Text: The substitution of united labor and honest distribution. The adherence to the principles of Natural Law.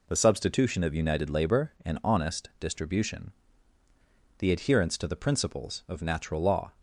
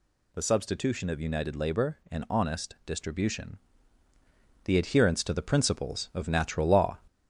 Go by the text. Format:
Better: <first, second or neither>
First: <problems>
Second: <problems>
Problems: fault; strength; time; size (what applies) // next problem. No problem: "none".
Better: first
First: none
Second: gets louder; slight; throughout; 3 dB